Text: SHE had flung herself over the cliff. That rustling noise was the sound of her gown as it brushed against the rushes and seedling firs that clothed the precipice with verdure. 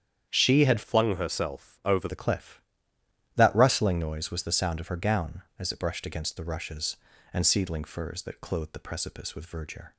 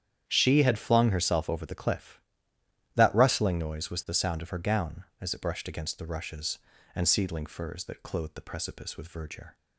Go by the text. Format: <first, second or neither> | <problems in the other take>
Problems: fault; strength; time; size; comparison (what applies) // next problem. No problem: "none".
second | starts louder than the rest; strong; until 1.3 s; 8.5 dB; strong in the second // changes voice from "flung" to "over"; from 0.8 to 2.0 s; 1.2 s long